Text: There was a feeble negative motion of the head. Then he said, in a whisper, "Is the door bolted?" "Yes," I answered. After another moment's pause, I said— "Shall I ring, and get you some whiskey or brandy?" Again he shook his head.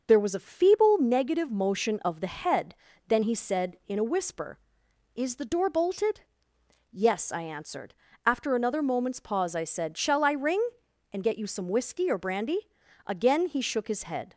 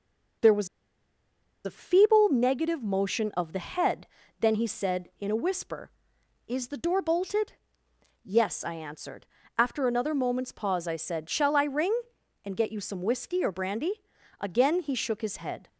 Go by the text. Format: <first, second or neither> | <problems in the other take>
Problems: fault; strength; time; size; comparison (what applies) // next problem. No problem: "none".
first | pauses between "was" and "a"; at 0.6 s; 0.98 s long